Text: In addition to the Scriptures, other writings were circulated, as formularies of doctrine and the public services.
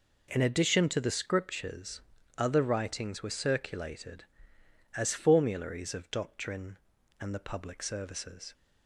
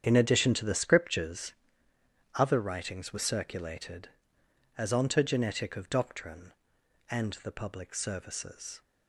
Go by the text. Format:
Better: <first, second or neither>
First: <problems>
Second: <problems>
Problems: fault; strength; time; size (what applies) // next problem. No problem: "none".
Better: first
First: none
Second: starts louder than the rest; strong; until 1.0 s; 8.5 dB // says "ontogenetic" for "formularies"; at 4.9 s